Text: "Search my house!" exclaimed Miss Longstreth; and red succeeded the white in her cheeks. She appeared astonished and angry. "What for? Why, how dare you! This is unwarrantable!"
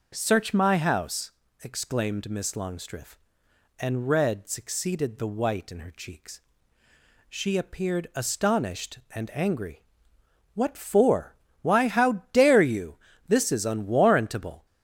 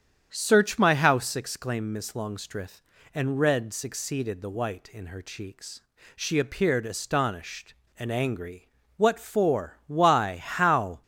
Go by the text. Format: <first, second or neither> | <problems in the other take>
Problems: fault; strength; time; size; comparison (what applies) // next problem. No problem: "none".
first | starts louder than the rest; strong; until 1.3 s; 8.5 dB // stops before "dare you This is unwarrantable"; at 11.0 s